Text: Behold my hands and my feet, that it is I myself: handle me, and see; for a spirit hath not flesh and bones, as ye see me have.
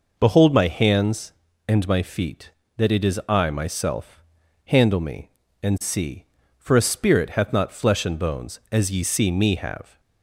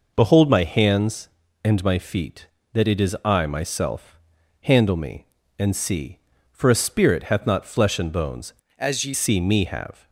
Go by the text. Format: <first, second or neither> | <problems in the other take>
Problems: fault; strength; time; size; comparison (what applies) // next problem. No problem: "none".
first | changes voice from "as" to "ye"; from 8.7 to 9.1 s; 0.4 s long